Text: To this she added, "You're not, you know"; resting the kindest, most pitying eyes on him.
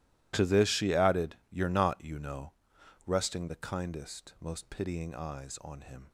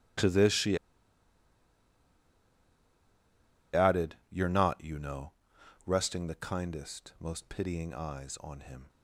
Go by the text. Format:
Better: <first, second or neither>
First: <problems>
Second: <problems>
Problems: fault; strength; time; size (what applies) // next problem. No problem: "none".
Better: first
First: none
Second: pauses between "she" and "added"; strong; at 0.7 s; 2.9 s long